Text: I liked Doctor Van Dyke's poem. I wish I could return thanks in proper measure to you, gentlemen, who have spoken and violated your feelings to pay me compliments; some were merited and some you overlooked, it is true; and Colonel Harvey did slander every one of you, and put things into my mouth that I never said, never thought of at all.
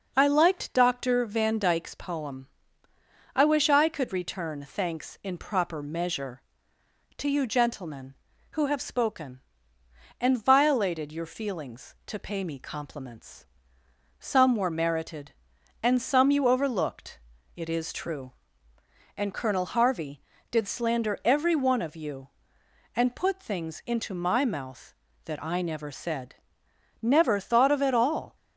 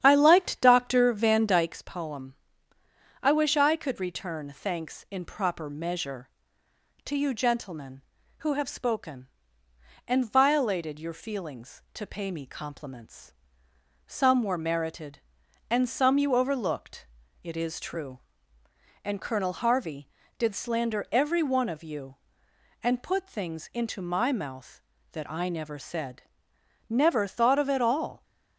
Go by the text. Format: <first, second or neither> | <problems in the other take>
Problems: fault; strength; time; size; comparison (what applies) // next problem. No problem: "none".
first | starts louder than the rest; strong; until 1.8 s; 9.5 dB